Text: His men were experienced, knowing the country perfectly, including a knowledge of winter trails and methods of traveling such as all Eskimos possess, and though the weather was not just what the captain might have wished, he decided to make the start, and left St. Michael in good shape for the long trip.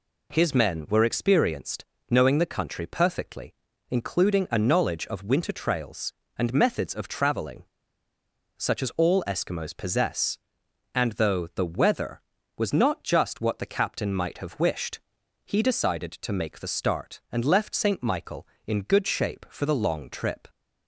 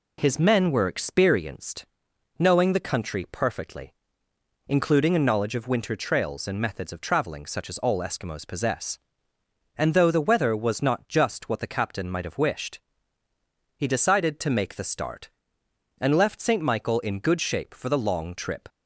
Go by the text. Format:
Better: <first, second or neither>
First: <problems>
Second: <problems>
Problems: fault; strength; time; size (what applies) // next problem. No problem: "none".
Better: second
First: pauses between "traveling" and "such"; noticeable; at 7.6 s; 0.90 s long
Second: none